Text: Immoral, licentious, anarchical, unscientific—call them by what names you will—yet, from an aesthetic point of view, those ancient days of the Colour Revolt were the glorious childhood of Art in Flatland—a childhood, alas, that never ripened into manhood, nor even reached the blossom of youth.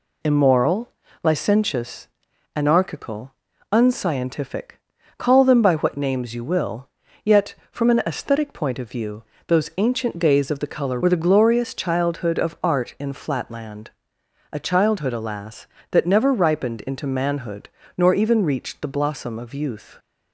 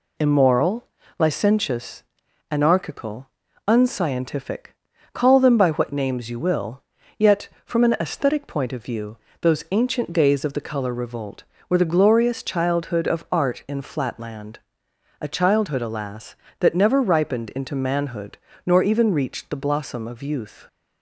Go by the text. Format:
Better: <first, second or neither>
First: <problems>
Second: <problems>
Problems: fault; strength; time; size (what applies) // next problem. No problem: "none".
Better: second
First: skips "Revolt"; at 11.0 s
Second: none